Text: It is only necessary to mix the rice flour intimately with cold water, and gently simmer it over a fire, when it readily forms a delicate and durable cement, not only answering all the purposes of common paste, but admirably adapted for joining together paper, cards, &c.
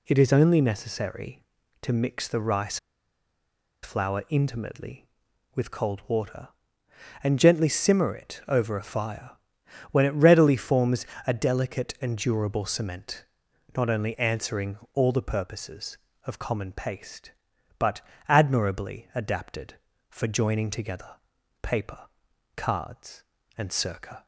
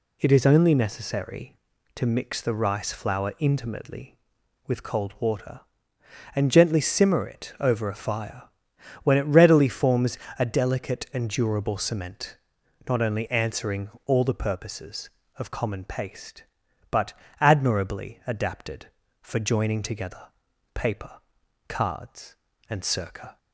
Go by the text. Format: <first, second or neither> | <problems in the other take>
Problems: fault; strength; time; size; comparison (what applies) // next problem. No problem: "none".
second | pauses between "rice" and "flour"; at 2.7 s; 1.0 s long // pauses between "forms" and "a"; slight; at 11.0 s; 0.18 s long; slight in the second // pauses between "answering" and "all"; slight; at 14.7 s; 0.16 s long; slight in the second // pauses between "but" and "admirably"; slight; at 18.0 s; 0.26 s long; slight in the second // pauses between "together" and "paper"; noticeable; at 21.1 s; 0.48 s long; noticeable in the second